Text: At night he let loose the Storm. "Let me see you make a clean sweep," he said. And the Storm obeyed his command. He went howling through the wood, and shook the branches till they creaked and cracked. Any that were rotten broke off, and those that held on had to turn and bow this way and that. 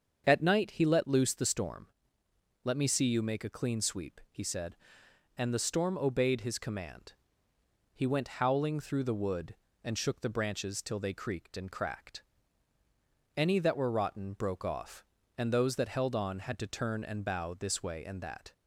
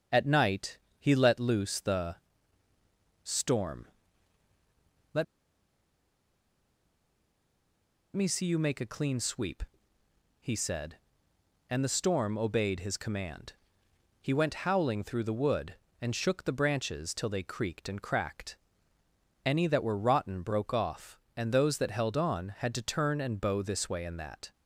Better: first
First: starts louder than the rest; until 1.2 s; 7 dB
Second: starts louder than the rest; until 1.3 s; 7 dB // pauses between "night" and "he"; slight; at 0.7 s; 0.22 s long // pauses between "the" and "Storm"; at 2.1 s; 1.0 s long // pauses between "Let" and "me"; strong; at 5.2 s; 2.9 s long

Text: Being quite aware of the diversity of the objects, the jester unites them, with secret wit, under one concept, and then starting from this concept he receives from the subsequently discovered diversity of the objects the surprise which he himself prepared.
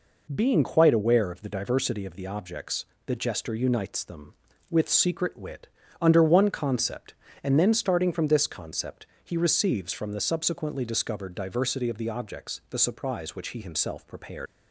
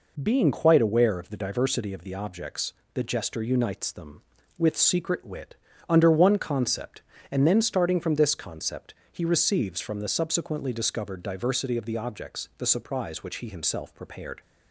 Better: second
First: pauses between "concept" and "he"; slight; at 9.0 s; 0.18 s long // leaves "prepared" unfinished; at 14.4 s; 65 ms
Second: pauses between "concept" and "he"; slight; at 8.9 s; 0.18 s long

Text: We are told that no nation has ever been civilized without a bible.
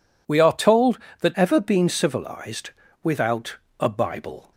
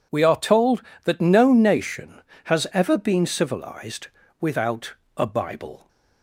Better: second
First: skips "no nation has"; at 1.3 s // pauses between "civilized" and "without"; slight; at 2.7 s; 0.32 s long // pauses between "without" and "a"; slight; at 3.5 s; 0.22 s long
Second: pauses between "civilized" and "without"; slight; at 4.0 s; 0.32 s long // pauses between "without" and "a"; slight; at 4.9 s; 0.22 s long

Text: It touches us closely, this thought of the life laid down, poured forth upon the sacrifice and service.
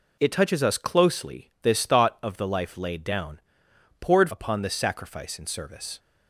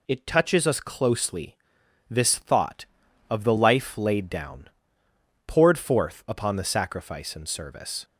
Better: second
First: skips "forth"; at 4.2 s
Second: none

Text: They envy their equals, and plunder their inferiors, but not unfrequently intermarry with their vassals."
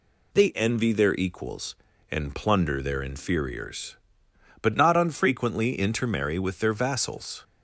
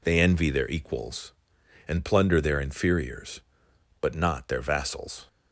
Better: first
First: none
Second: skips "unfrequently intermarry with"; at 4.4 s

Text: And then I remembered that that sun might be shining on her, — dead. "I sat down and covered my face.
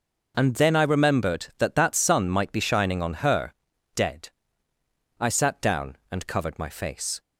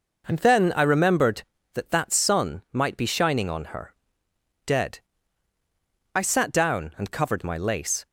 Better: first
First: none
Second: says "lace" for "face"; at 7.5 s

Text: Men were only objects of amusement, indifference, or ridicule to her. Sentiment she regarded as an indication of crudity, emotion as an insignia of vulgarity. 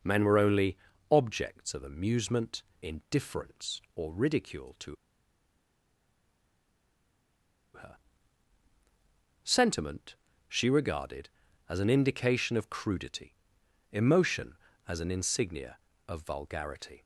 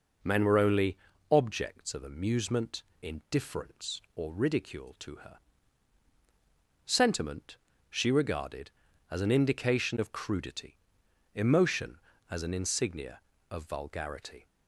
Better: second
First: pauses between "only" and "objects"; slight; at 0.7 s; 0.34 s long // pauses between "to" and "her"; strong; at 4.9 s; 2.7 s long // pauses between "Sentiment" and "she"; slight; at 10.1 s; 0.32 s long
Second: pauses between "only" and "objects"; slight; at 0.9 s; 0.34 s long // pauses between "Sentiment" and "she"; slight; at 7.5 s; 0.32 s long

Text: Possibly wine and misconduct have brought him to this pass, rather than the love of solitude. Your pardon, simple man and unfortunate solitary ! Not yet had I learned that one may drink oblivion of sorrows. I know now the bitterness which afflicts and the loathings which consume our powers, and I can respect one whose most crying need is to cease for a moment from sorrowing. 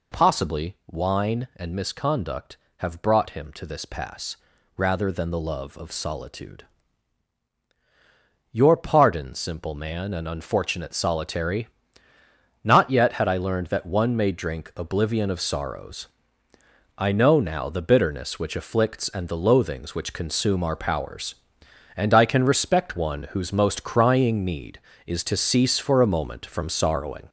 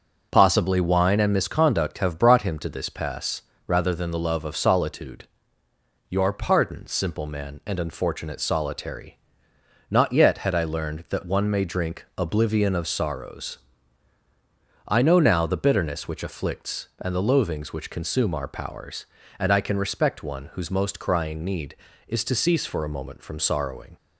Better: second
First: gets louder; noticeable; throughout; 5 dB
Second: none

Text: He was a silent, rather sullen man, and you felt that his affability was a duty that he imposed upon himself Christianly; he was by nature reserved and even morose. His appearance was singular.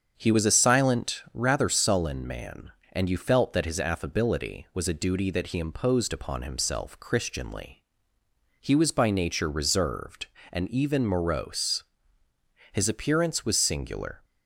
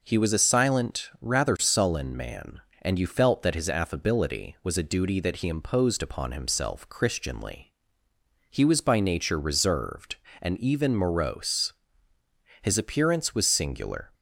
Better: second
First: starts louder than the rest; until 1.6 s; 7 dB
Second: none

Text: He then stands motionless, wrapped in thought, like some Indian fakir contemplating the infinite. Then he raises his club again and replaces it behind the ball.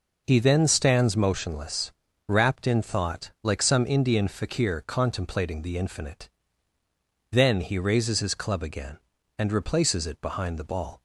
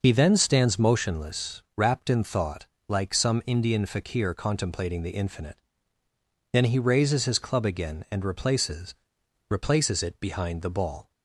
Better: first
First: none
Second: says "replaces" twice; at 9.5 s

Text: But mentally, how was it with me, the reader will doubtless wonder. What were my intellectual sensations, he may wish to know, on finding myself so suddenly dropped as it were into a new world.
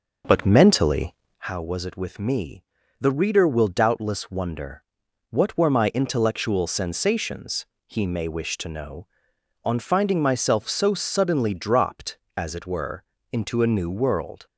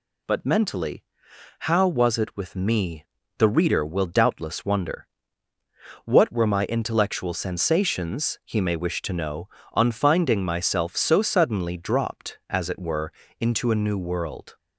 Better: second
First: starts louder than the rest; noticeable; until 1.5 s; 6 dB // pauses between "were" and "into"; slight; at 13.0 s; 0.28 s long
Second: pauses between "were" and "into"; slight; at 13.1 s; 0.28 s long

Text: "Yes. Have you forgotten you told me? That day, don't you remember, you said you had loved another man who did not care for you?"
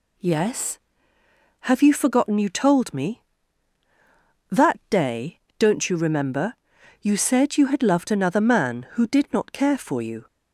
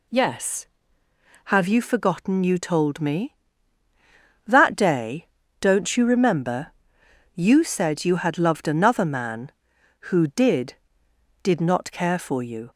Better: first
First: none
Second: says "did" twice; at 11.4 s

